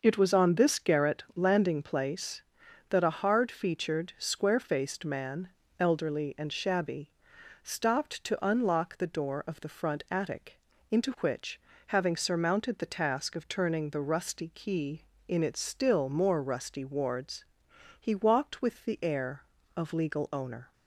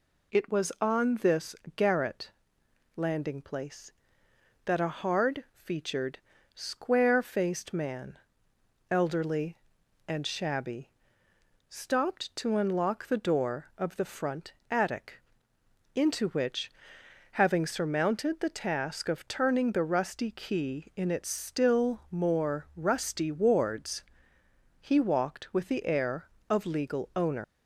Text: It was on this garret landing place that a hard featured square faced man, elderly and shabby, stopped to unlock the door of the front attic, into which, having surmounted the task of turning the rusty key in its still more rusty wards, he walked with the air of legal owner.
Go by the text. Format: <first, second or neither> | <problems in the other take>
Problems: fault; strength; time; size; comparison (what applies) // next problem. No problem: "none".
first | pauses between "this" and "garret"; slight; at 1.5 s; 0.22 s long // pauses between "garret" and "landing"; noticeable; at 2.3 s; 0.64 s long // pauses between "featured" and "square"; slight; at 6.1 s; 0.36 s long // pauses between "front" and "attic"; slight; at 14.5 s; 0.18 s long // leaves "owner" unfinished; at 27.4 s; 135 ms